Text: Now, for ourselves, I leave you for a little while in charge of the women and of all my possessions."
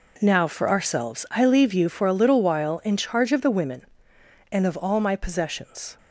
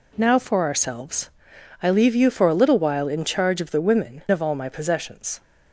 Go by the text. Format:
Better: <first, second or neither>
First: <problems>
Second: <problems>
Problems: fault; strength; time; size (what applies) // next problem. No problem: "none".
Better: first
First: none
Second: skips "and"; at 4.2 s